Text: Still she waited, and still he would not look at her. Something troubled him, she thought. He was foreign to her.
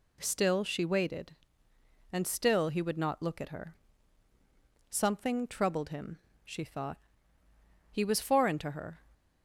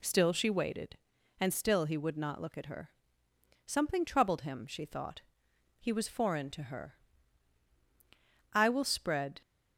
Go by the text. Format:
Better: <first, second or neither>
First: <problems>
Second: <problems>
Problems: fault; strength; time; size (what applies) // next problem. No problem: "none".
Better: first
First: none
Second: goes on to say "I will spread"; noticeable; from 8.5 s on; 0.90 s long